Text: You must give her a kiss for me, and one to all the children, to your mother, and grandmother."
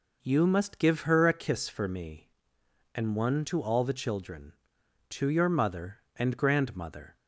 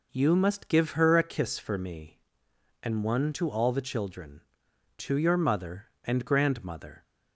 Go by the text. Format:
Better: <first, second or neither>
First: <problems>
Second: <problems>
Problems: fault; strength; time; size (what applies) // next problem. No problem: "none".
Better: neither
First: none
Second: none